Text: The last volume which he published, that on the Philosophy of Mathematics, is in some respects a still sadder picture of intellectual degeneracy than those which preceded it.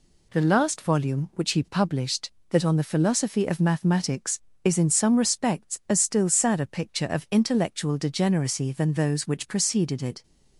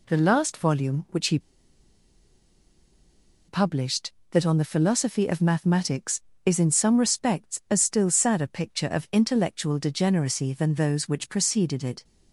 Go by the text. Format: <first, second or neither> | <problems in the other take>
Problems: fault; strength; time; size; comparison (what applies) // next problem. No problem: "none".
first | pauses between "he" and "published"; strong; at 1.3 s; 2.0 s long